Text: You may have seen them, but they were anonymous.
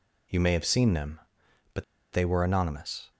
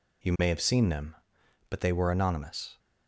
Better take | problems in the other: second | pauses between "but" and "they"; slight; at 1.8 s; 0.28 s long

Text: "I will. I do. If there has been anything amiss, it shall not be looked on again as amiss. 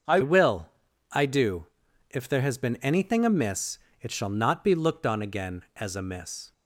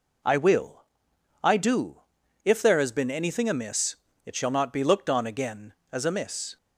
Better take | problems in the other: second | starts louder than the rest; until 1.5 s; 6.5 dB // changes voice at "will"; from 0.2 s on; 6.3 s long

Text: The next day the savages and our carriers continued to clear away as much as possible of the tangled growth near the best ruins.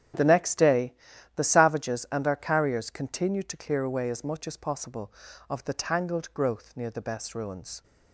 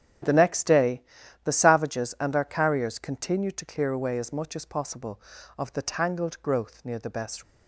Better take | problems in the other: first | starts louder than the rest; strong; until 1.6 s; 9 dB; strong in the first // pauses between "day" and "the"; at 1.0 s; 0.42 s long; also in the first // stops before "ruins"; at 7.4 s

